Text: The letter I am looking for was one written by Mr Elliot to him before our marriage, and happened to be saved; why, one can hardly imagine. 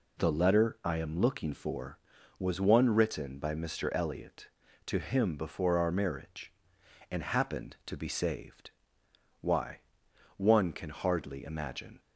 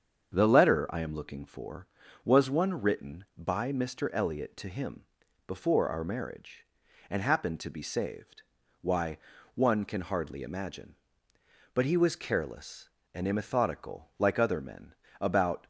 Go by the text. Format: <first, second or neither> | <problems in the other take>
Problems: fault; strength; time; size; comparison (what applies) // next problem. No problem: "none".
first | starts louder than the rest; strong; until 1.3 s; 7 dB // pauses between "him" and "before"; at 5.0 s; 0.44 s long // goes on to say "But he was careless and immethodical like other men about"; strong; from 11.7 s on; 3.9 s long